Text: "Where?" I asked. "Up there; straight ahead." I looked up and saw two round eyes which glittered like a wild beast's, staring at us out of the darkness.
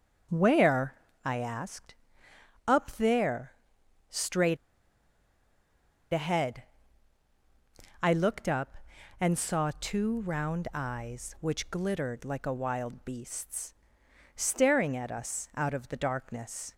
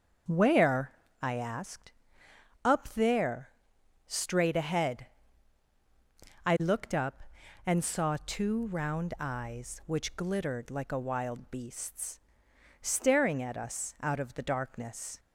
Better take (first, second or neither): second